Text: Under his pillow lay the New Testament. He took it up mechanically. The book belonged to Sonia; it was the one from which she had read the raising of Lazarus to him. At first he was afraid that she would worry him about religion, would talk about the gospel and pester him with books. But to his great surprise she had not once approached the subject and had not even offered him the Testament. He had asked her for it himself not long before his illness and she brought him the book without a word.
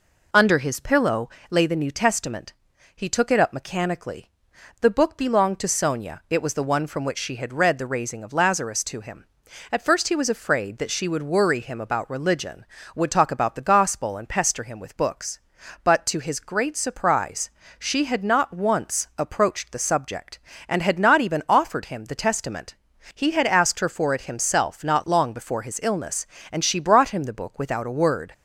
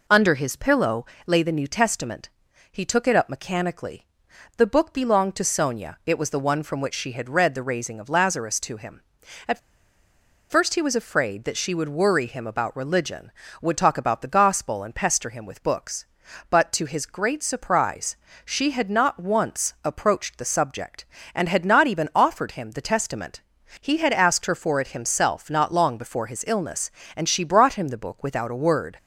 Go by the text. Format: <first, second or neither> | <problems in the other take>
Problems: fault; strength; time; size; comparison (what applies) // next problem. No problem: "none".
first | pauses between "pillow" and "lay"; slight; at 1.0 s; 0.20 s long; slight in the first // pauses between "At" and "first"; noticeable; at 9.5 s; 0.90 s long // pauses between "surprise" and "she"; slight; at 18.1 s; 0.26 s long; slight in the first